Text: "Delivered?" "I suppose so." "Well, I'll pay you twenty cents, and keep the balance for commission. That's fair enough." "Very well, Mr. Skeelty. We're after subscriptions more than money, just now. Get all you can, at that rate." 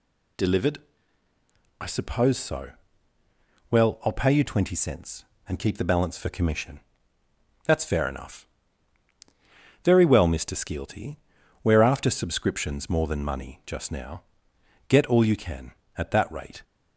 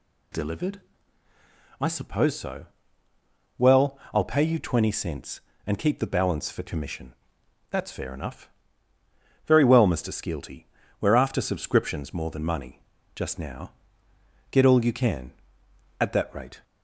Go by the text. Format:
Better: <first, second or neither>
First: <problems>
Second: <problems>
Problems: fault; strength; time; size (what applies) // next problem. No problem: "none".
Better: neither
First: none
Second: none